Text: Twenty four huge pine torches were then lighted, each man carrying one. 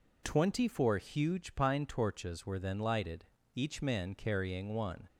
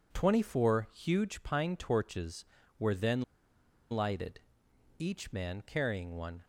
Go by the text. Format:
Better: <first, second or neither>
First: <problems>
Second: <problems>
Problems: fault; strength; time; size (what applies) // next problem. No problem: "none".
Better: first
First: none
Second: pauses between "then" and "lighted"; noticeable; at 3.2 s; 0.69 s long